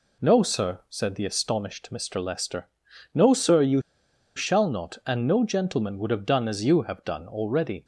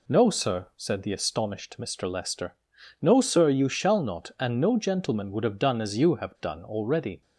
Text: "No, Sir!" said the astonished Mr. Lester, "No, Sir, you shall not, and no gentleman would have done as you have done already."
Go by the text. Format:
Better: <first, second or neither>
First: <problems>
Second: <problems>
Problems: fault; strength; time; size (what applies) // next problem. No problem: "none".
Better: second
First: pauses between "you" and "shall"; noticeable; at 3.8 s; 0.55 s long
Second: none